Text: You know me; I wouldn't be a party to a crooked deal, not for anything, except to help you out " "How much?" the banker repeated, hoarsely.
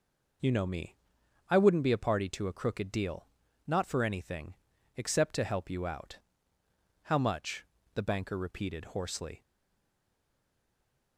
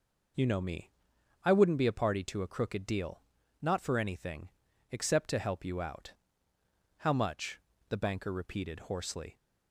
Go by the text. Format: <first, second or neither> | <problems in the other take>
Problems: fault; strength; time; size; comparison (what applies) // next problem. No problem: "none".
second | stays silent after the last word; noticeable; from 9.4 s on; 1.7 s long